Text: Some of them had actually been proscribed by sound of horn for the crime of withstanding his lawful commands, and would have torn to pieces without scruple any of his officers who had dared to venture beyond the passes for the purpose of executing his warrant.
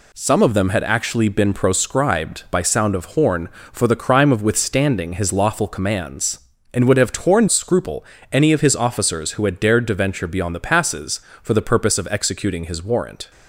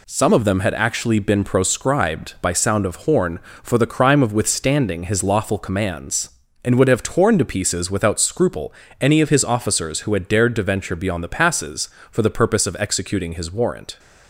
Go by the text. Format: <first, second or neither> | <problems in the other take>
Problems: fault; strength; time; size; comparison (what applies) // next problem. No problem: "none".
second | skips "to pieces without"; at 7.4 s // pauses between "scruple" and "any"; slight; at 8.0 s; 0.26 s long; slight in the second